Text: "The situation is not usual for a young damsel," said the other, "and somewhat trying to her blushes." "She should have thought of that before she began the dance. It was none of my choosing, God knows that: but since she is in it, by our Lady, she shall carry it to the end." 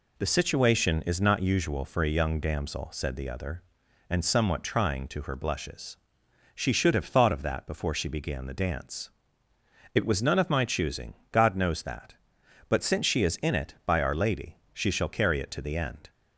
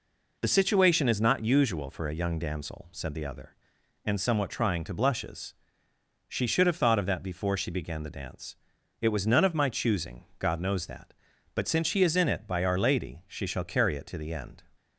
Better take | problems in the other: first | skips "her"; at 4.9 s

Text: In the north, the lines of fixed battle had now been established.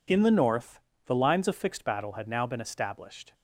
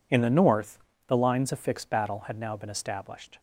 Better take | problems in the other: neither | none

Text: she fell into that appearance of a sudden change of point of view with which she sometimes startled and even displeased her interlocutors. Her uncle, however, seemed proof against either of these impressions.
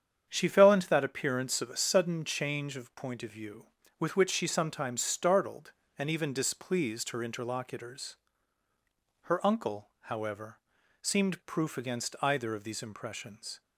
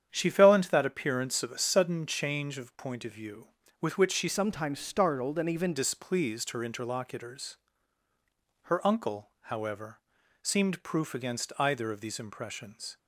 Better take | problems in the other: first | starts louder than the rest; strong; until 1.1 s; 8.5 dB; strong in the first // changes voice from "sometimes" to "even"; from 4.2 to 5.7 s; 1.5 s long

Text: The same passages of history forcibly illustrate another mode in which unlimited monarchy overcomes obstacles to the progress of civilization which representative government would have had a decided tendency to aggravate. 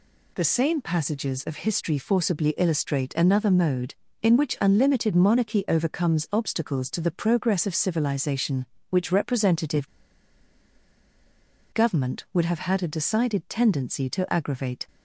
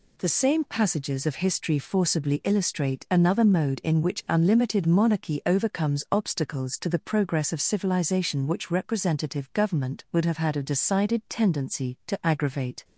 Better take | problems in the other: second | pauses between "representative" and "government"; strong; at 9.8 s; 1.8 s long

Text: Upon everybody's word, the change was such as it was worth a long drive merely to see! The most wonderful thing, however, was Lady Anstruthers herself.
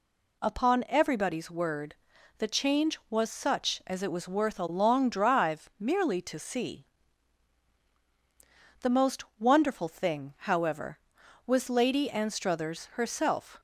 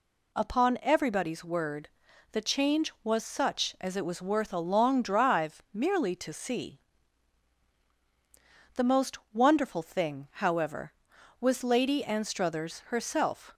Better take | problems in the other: neither | pauses between "most" and "wonderful"; slight; the same in both

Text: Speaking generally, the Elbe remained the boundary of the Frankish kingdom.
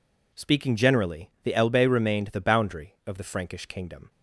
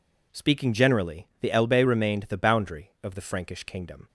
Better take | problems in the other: neither | none

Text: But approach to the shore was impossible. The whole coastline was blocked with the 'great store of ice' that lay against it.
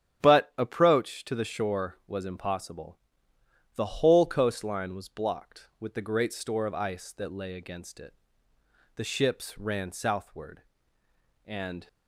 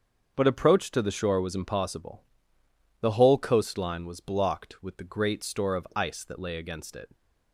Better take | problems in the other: second | starts louder than the rest; strong; until 1.2 s; 9.5 dB; also in the second // goes on to say "The ships ran southward and"; strong; from 8.9 s on; 2.9 s long

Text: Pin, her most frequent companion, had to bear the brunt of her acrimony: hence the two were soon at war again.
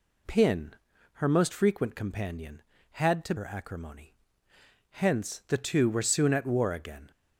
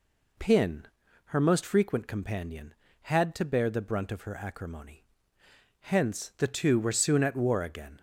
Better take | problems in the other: second | skips "bear the brunt of"; at 3.3 s

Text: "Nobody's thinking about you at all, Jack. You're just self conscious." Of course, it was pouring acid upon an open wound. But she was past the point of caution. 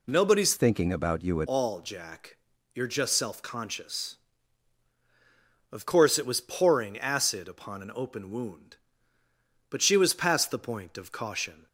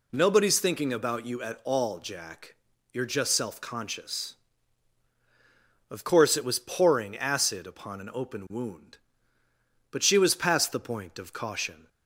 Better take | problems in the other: second | changes voice from "thinking" to "at"; from 0.5 to 1.4 s; 0.9 s long

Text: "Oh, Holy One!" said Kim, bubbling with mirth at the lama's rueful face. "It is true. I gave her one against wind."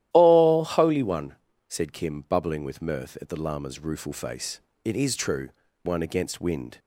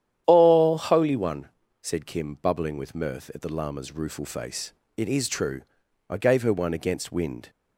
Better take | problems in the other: second | starts louder than the rest; strong; until 1.1 s; 13 dB; strong in the second // skips "I gave her"; at 5.6 s

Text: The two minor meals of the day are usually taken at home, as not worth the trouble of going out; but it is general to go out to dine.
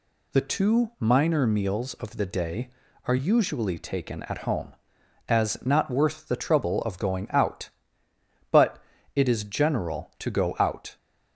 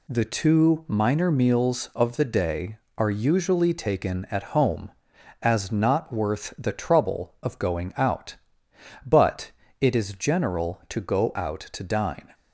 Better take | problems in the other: second | pauses between "but" and "it"; at 8.7 s; 0.38 s long; slight in the second // stops before "to dine"; at 10.9 s

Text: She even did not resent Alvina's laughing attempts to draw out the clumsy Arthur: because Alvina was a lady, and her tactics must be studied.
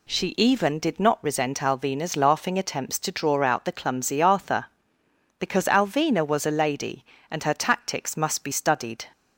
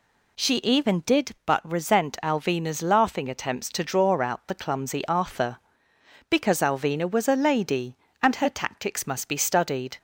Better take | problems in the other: first | says "but" for "not"; at 1.4 s

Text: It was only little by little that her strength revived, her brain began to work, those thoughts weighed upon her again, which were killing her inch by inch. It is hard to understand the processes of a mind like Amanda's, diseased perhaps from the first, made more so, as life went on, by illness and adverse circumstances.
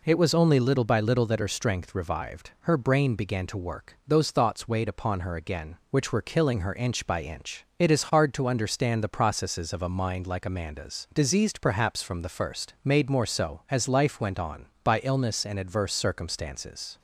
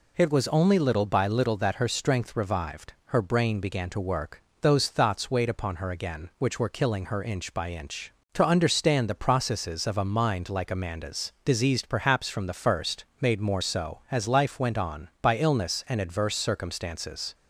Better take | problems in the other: first | skips "It is hard"; at 8.2 s

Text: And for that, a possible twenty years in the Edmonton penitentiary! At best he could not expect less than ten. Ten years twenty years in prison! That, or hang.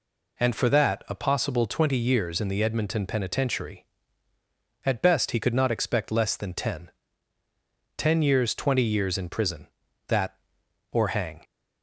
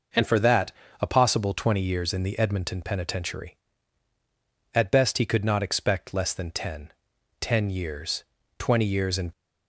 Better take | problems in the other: first | pauses between "years" and "twenty"; slight; at 8.2 s; 0.34 s long // stops before "prison That or hang"; at 9.3 s

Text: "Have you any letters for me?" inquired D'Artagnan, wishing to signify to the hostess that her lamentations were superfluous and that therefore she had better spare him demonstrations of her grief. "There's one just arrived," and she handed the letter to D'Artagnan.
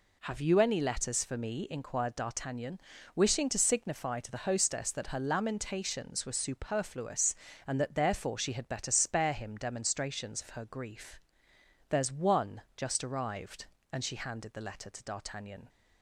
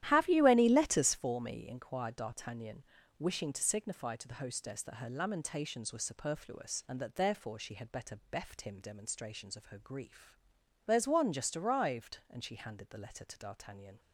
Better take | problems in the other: first | starts louder than the rest; strong; until 1.0 s; 12.5 dB // says "beft" for "spare"; at 8.2 s

